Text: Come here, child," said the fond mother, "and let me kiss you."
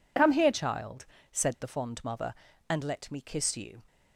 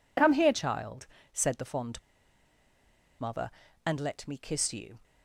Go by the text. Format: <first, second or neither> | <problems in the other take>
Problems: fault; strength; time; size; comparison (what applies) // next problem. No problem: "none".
first | pauses between "fond" and "mother"; at 1.9 s; 1.2 s long